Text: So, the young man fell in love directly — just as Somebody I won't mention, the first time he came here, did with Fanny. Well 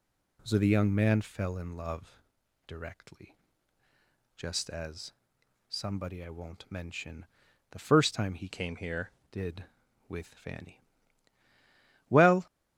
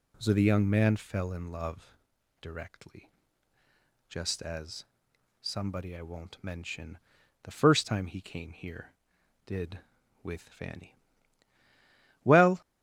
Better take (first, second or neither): second